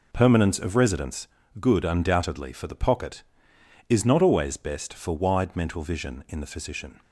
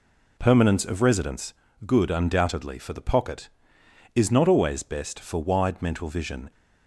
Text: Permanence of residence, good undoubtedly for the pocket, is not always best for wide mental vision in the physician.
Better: first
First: none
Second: stops before "in the physician"; at 6.5 s

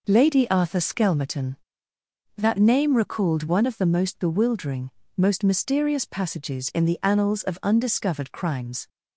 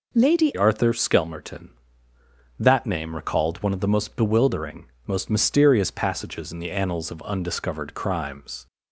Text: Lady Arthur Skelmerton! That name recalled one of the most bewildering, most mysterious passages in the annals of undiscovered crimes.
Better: first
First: none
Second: changes voice at "Arthur"; from 0.5 s on; 8.1 s long

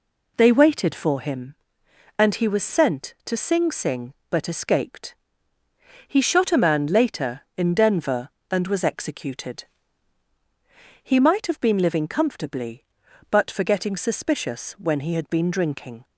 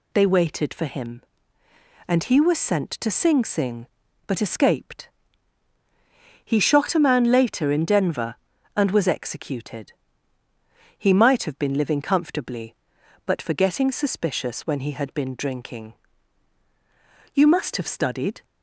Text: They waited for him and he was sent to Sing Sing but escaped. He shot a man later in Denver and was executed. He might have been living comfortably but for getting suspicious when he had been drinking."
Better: first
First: none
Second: goes on to say "You must have studied"; noticeable; from 17.3 s on; 1.0 s long

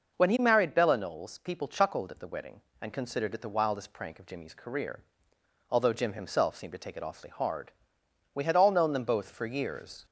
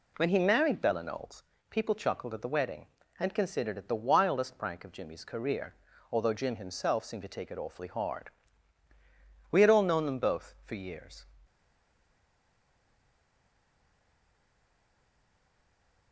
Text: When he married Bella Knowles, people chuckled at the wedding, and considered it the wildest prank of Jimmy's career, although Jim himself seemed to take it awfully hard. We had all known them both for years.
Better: first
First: none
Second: stays silent after the last word; strong; from 11.4 s on; 4.7 s long

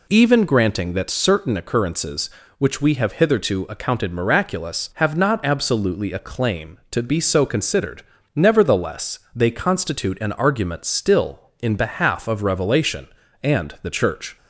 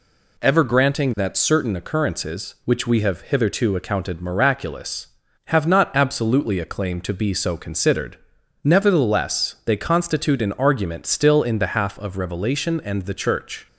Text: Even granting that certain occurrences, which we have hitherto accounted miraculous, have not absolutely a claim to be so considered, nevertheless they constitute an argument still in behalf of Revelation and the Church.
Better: first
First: none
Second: says "Ever" for "Even"; at 0.3 s

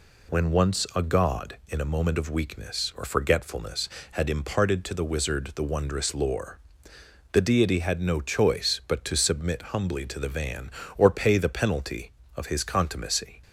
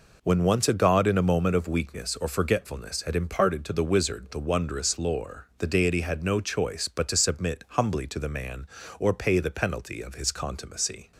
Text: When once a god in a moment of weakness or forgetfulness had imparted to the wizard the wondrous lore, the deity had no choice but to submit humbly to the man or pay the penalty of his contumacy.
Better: second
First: says "van" for "man"; at 10.2 s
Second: none

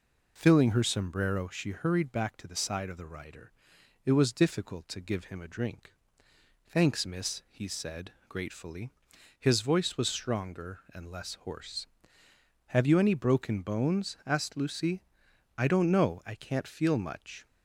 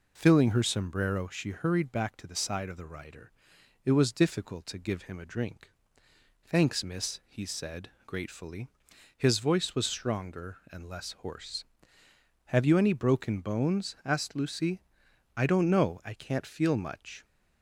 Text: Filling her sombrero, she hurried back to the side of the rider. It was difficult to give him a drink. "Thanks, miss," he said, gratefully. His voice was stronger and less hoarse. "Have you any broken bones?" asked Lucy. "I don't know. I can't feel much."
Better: neither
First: none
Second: none

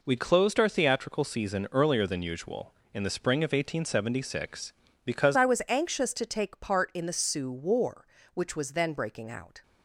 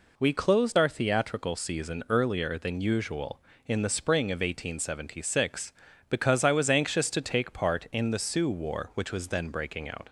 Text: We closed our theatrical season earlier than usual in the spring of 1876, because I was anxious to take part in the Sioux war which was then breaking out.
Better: second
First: changes voice at "I"; from 5.3 s on; 4.3 s long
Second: none

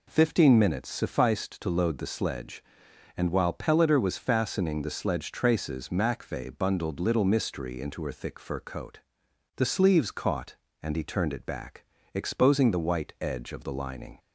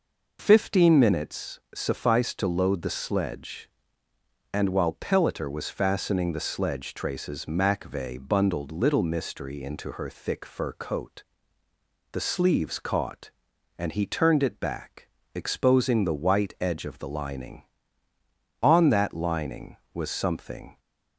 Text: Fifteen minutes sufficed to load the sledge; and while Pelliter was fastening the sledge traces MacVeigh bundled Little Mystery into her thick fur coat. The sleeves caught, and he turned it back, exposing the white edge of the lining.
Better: first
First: none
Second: goes on to say "On that lining was something"; strong; from 18.6 s on; 2.1 s long

